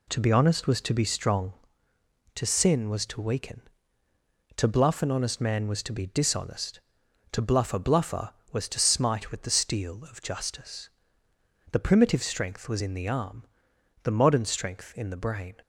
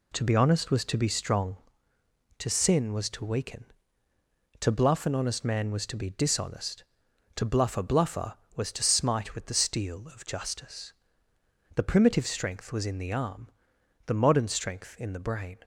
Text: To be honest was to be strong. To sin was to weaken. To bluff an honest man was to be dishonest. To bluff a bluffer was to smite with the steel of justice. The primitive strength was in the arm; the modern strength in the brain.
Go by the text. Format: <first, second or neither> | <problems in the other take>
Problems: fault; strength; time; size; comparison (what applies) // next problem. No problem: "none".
neither | none